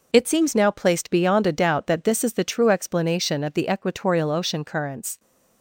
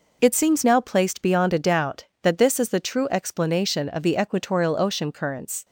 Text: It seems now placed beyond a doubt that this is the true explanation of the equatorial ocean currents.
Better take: neither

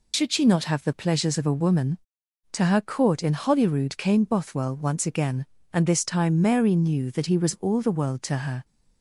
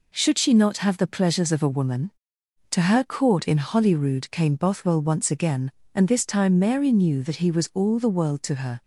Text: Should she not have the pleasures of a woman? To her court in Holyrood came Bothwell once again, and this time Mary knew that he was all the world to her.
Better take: second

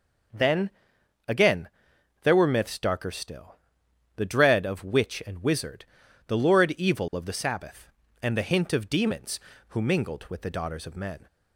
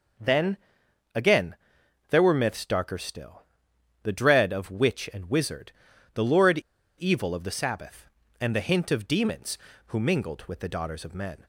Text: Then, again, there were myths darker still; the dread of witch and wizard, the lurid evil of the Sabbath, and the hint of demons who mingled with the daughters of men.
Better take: first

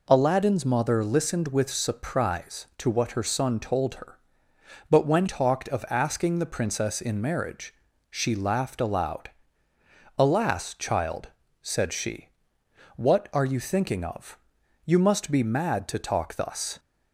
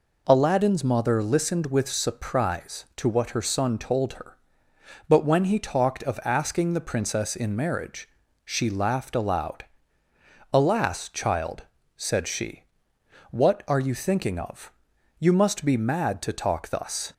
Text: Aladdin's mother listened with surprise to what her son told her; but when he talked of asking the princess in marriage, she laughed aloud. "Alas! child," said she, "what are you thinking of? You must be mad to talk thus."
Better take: second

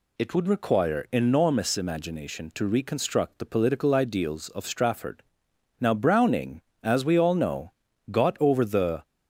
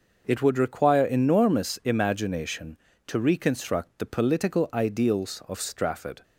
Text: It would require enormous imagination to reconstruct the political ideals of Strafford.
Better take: second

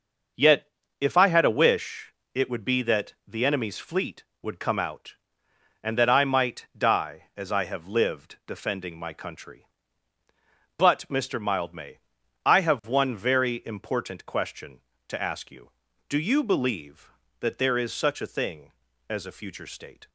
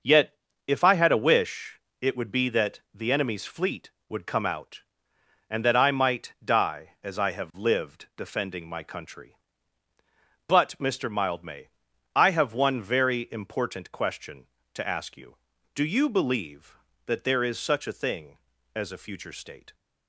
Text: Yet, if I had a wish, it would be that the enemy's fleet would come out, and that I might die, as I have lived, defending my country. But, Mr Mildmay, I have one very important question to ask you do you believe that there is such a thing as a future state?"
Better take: neither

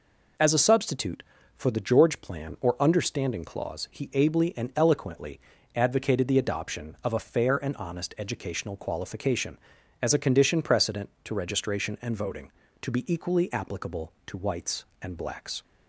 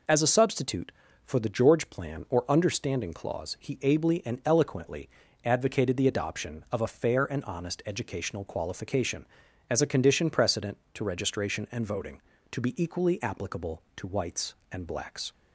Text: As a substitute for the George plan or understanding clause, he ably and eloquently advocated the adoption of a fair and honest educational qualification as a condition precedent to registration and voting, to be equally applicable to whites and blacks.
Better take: neither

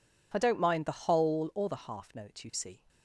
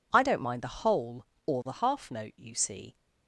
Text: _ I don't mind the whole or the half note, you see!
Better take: neither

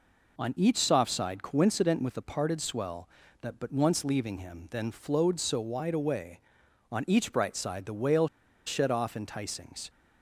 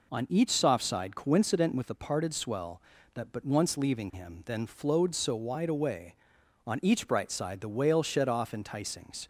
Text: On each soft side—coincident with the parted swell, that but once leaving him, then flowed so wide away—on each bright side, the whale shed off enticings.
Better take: second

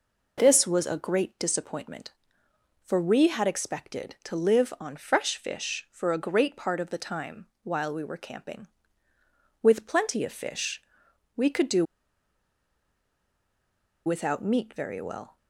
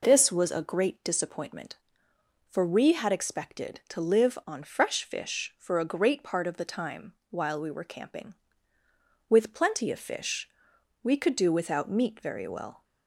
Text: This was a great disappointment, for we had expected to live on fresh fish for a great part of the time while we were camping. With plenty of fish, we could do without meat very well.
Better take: second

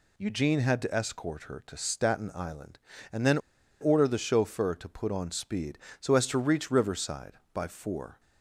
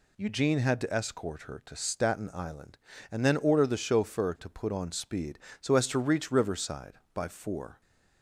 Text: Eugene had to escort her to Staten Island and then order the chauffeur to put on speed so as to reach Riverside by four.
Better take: second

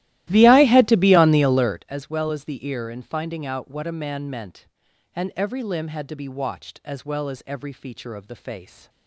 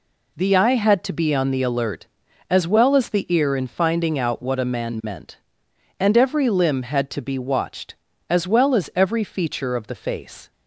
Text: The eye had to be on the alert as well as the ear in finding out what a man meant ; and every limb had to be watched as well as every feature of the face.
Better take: second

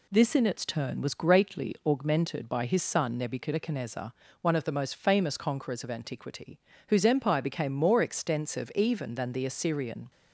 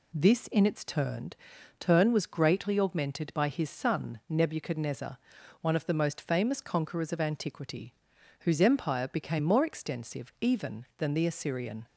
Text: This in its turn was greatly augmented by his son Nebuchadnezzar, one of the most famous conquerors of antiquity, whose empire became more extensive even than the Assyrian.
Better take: first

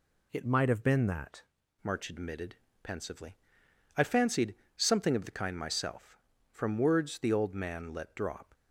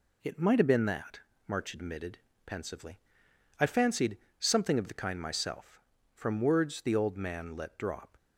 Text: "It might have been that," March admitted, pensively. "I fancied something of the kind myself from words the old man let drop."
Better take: second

